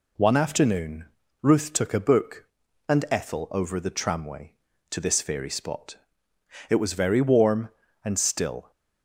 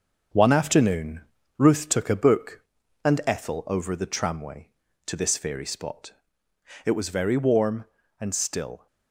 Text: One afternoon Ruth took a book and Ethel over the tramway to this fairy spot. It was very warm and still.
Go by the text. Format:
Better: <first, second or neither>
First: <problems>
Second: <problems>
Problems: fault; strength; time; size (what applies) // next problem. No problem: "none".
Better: first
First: pauses between "afternoon" and "Ruth"; at 1.0 s; 0.38 s long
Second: gets quieter; noticeable; throughout; 6 dB // pauses between "afternoon" and "Ruth"; at 1.2 s; 0.38 s long